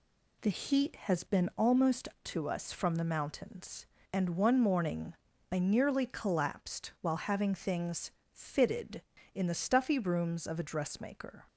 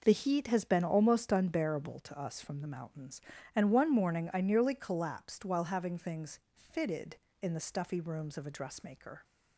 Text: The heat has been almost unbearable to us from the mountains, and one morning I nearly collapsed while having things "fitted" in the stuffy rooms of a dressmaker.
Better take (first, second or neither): second